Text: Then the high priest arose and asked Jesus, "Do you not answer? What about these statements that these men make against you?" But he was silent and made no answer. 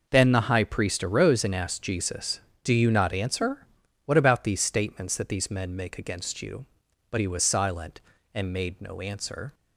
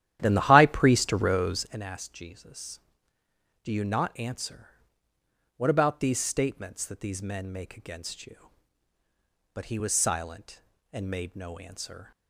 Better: first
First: none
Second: starts louder than the rest; strong; until 1.8 s; 12 dB

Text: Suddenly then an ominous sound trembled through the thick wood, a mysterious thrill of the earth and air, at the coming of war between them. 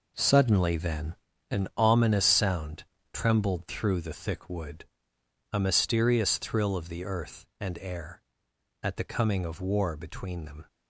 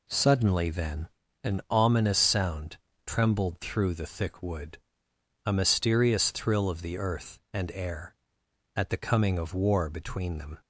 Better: second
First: gets quieter; strong; throughout; 9.5 dB // pauses between "then" and "an"; slight; at 1.1 s; 0.36 s long // pauses between "sound" and "trembled"; slight; at 2.8 s; 0.26 s long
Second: pauses between "then" and "an"; slight; at 1.0 s; 0.36 s long // pauses between "sound" and "trembled"; slight; at 2.7 s; 0.26 s long

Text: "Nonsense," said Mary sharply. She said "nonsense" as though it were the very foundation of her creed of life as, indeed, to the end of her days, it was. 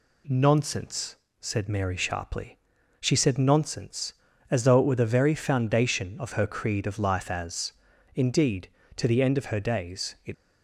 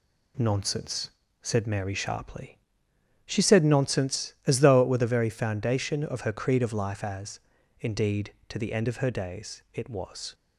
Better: second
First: stops before "was"; at 10.3 s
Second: none

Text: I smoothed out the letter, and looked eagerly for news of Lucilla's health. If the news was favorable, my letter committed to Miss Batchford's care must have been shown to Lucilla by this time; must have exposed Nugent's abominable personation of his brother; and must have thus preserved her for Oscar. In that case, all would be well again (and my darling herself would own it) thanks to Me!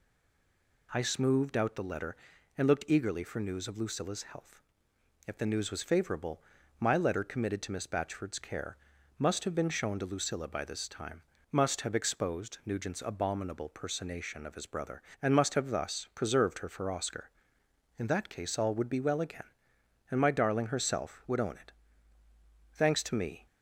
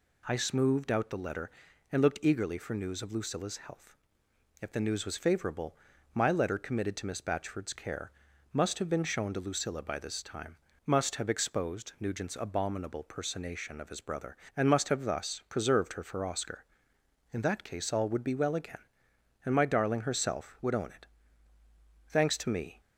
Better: second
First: stays silent before the first word; slight; until 0.8 s; 0.8 s long // pauses between "care" and "must"; at 8.7 s; 0.42 s long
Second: pauses between "care" and "must"; at 8.1 s; 0.42 s long

